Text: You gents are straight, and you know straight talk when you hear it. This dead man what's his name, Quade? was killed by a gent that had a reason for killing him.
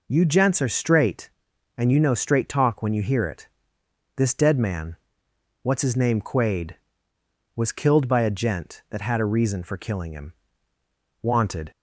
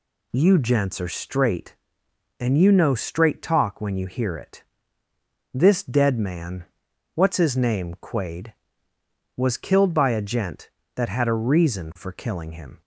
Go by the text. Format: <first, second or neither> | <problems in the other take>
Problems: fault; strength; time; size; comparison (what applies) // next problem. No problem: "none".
second | pauses between "man" and "what's"; noticeable; at 4.9 s; 0.68 s long; noticeable in the second // goes on to say "Wanted"; slight; from 11.2 s on; 0.48 s long